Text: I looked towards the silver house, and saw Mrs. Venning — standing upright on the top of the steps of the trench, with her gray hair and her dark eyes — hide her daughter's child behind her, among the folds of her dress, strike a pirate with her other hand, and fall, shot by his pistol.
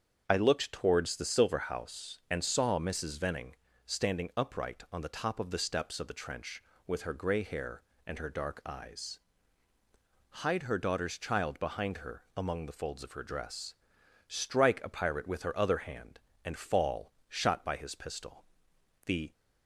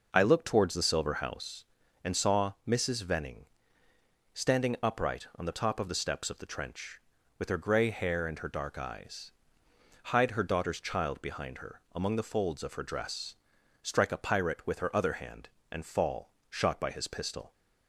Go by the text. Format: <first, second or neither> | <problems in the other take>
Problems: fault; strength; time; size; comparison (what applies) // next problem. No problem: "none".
second | starts louder than the rest; strong; until 1.2 s; 7.5 dB // goes on to say "The"; slight; from 19.0 s on; 0.26 s long